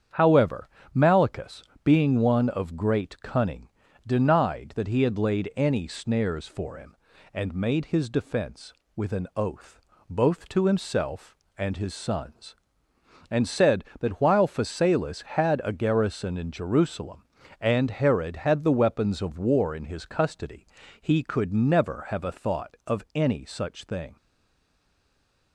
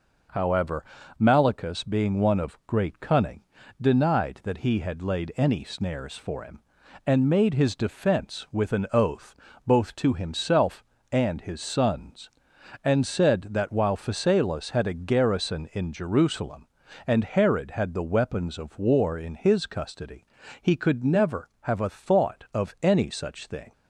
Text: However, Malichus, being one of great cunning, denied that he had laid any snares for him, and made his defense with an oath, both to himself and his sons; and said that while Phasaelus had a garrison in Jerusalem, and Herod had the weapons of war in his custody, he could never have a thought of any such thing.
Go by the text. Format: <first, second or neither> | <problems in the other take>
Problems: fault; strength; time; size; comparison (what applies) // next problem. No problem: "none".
second | starts louder than the rest; strong; until 1.3 s; 8.5 dB // stays silent after the last word; noticeable; from 24.1 s on; 1.4 s long